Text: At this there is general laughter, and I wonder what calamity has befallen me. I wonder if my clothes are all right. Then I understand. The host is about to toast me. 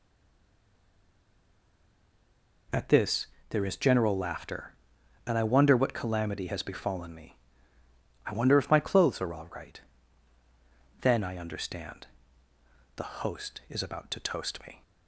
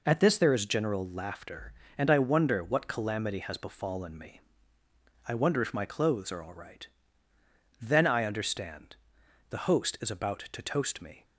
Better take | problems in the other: second | stays silent before the first word; strong; until 2.6 s; 2.6 s long // pauses between "this" and "there"; slight; at 3.2 s; 0.24 s long

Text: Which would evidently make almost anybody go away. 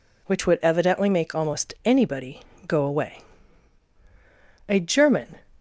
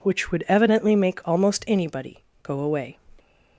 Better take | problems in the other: second | pauses between "anybody" and "go"; slight; at 2.4 s; 0.24 s long; slight in the second // goes on to say "A German"; noticeable; from 4.6 s on; 0.70 s long

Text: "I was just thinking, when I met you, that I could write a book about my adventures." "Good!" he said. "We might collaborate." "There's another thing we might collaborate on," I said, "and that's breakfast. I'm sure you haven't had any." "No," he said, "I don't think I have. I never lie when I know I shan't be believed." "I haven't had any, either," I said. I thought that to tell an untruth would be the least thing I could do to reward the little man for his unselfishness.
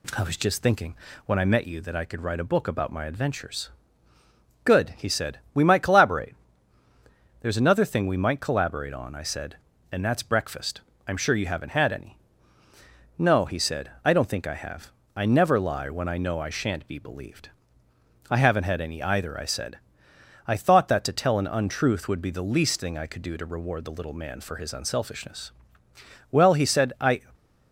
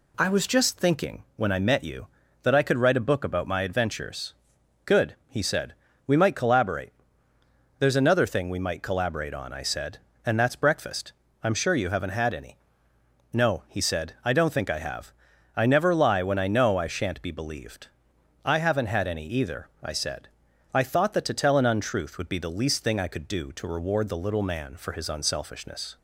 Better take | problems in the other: second | goes on to say "Well he said I"; noticeable; from 26.2 s on; 0.92 s long // stays silent after the last word; slight; from 27.1 s on; 0.6 s long

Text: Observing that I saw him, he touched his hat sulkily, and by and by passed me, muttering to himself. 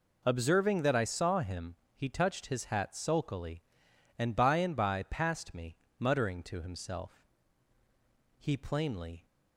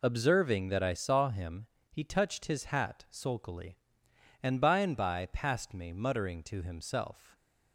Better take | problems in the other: second | goes on to say "He plainly"; noticeable; from 8.3 s on; 0.88 s long

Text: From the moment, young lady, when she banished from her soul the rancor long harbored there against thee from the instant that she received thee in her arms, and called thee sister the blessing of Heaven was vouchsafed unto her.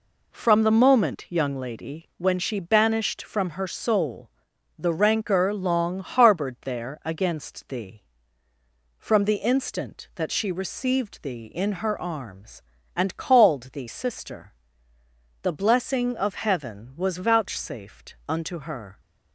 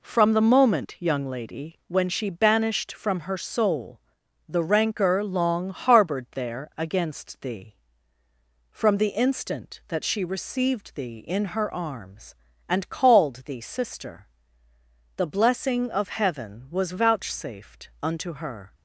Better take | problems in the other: neither | pauses between "soul" and "the"; noticeable; the same in both // pauses between "sister" and "the"; noticeable; the same in both

